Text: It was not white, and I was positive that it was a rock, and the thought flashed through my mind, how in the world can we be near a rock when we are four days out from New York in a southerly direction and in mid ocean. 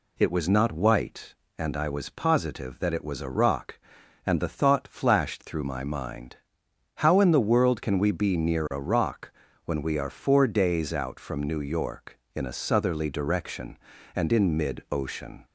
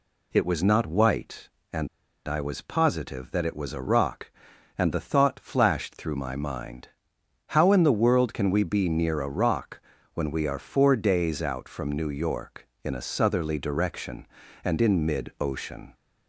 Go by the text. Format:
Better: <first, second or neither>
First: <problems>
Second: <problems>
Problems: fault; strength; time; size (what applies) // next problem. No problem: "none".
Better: first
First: pauses between "rock" and "when"; slight; at 9.3 s; 0.32 s long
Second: pauses between "and" and "I"; at 1.8 s; 0.40 s long // pauses between "rock" and "when"; slight; at 9.8 s; 0.32 s long